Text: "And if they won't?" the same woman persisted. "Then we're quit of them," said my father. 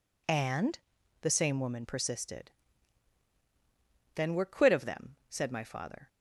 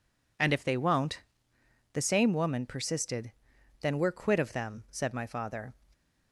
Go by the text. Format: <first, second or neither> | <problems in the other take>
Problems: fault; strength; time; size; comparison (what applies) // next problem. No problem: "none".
second | skips "if they won't"; at 0.9 s